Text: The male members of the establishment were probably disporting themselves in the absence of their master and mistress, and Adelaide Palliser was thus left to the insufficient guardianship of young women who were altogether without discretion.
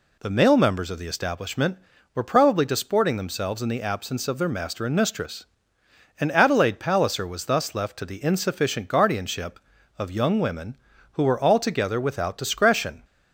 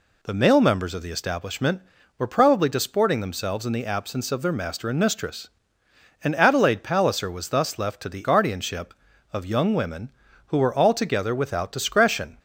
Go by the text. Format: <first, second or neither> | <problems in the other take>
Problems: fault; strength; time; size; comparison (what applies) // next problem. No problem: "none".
first | skips "insufficient"; at 8.2 s